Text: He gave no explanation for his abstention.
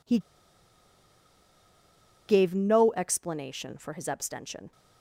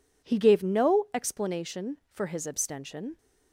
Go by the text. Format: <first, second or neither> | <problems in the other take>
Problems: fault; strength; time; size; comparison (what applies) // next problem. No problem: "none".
second | pauses between "He" and "gave"; strong; at 0.1 s; 2.0 s long